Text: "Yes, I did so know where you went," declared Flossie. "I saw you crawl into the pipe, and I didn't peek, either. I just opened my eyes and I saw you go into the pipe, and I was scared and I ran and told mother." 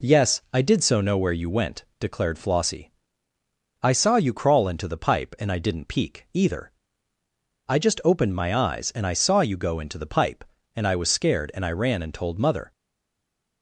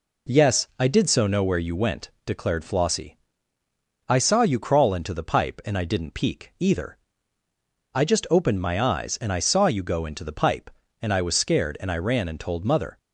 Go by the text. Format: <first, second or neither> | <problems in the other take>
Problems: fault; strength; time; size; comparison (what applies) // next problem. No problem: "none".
second | stays silent after the last word; slight; from 12.7 s on; 0.9 s long